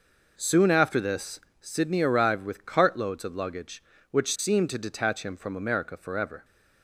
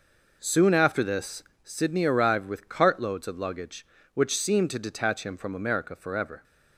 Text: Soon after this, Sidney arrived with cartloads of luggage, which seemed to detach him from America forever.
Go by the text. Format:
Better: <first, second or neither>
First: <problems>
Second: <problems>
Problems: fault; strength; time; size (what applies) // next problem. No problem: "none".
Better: neither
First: none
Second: none